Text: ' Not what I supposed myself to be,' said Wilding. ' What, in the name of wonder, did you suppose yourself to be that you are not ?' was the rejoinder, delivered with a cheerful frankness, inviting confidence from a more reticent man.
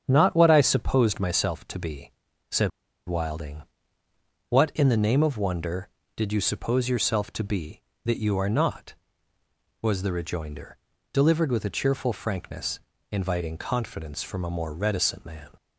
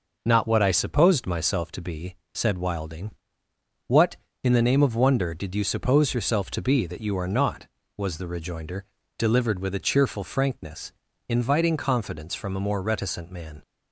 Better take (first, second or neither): second